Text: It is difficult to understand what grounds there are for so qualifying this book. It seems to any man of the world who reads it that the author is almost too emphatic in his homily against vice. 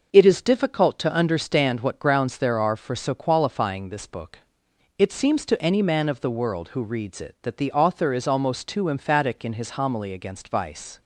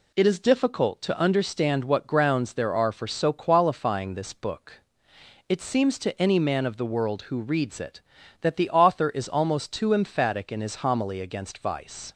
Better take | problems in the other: neither | none

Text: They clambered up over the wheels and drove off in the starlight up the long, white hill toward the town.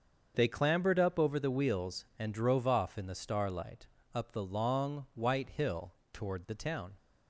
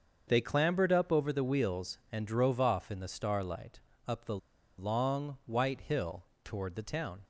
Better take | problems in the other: first | starts louder than the rest; until 1.2 s; 6.5 dB; also in the first // pauses between "starlight" and "up"; slight; at 3.8 s; 0.26 s long; slight in the first // pauses between "the" and "long"; at 4.3 s; 0.41 s long // pauses between "hill" and "toward"; slight; at 6.2 s; 0.18 s long; slight in the first

